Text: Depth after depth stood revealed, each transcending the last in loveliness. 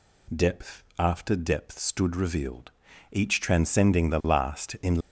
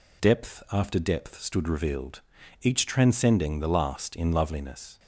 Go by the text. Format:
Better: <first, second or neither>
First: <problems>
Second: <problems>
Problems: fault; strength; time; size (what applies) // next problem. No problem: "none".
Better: second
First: pauses between "Depth" and "after"; slight; at 0.8 s; 0.16 s long // stops before "loveliness"; at 5.0 s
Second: none